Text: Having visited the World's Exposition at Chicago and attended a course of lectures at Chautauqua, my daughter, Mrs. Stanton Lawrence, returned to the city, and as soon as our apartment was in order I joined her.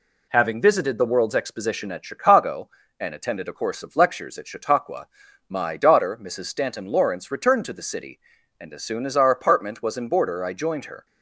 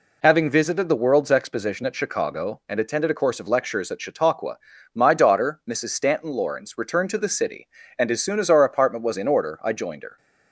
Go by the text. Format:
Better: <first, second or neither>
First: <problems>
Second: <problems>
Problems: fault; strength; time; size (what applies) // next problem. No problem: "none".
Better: second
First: says "border" for "order"; at 10.0 s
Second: none